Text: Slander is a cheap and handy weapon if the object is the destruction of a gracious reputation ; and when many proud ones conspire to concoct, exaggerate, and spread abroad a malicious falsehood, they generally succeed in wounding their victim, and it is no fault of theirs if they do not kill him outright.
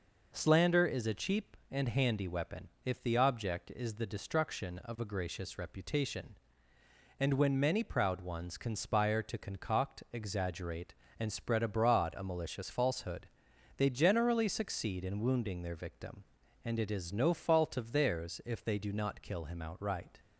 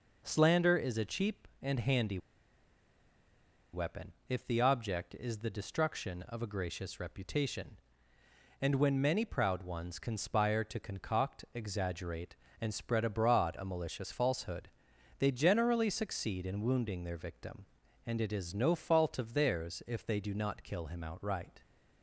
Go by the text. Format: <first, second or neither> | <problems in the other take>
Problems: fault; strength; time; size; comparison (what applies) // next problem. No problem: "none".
first | pauses between "handy" and "weapon"; strong; at 2.1 s; 1.5 s long // pauses between "weapon" and "if"; slight; at 4.1 s; 0.16 s long; slight in the first